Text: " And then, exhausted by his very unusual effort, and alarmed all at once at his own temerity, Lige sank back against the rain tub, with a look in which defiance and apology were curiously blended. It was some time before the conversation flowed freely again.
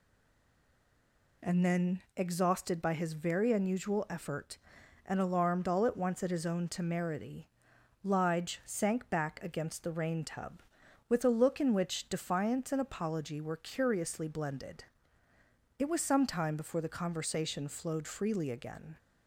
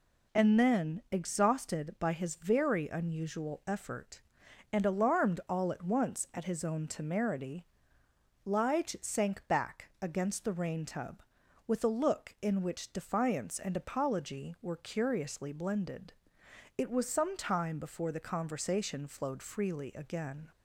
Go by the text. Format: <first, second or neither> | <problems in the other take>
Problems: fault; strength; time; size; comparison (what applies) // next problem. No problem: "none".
second | stays silent before the first word; noticeable; until 1.3 s; 1.3 s long